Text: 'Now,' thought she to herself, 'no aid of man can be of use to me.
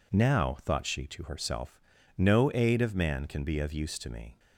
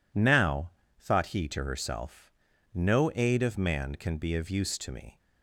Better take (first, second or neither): first